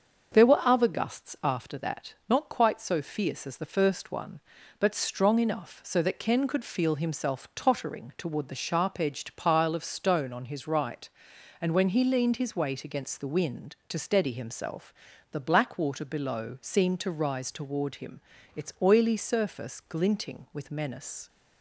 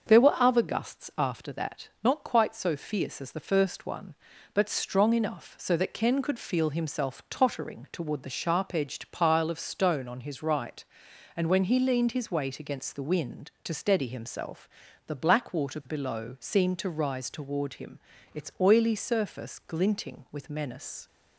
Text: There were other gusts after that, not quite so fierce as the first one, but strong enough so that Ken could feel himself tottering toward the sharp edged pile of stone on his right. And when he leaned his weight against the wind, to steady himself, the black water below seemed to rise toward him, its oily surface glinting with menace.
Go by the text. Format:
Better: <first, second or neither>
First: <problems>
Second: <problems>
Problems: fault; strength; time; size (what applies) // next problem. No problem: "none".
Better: neither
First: starts louder than the rest; until 1.4 s; 6.5 dB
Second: starts louder than the rest; until 1.2 s; 6.5 dB